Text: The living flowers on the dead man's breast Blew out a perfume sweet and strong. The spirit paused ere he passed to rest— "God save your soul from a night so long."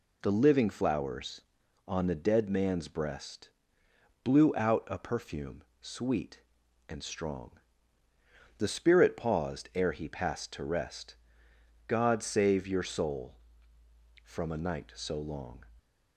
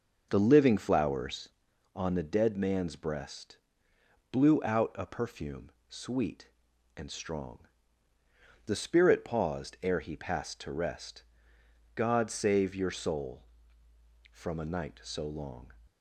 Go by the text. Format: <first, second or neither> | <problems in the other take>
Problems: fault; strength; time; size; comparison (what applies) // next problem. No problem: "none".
first | starts louder than the rest; until 1.5 s; 6.5 dB // pauses between "breast" and "Blew"; noticeable; at 3.5 s; 0.74 s long; noticeable in the first // pauses between "perfume" and "sweet"; slight; at 5.7 s; 0.18 s long; slight in the first